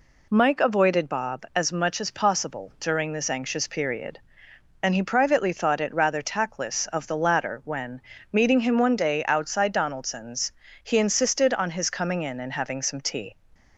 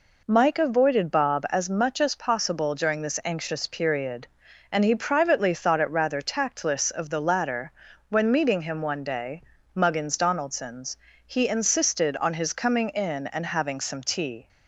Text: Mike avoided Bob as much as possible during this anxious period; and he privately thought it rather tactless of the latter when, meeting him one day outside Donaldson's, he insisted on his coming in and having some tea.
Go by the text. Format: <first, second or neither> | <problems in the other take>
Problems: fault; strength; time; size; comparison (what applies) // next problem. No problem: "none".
first | pauses between "latter" and "when"; at 7.6 s; 0.38 s long // says "muggins" for "outside"; at 9.7 s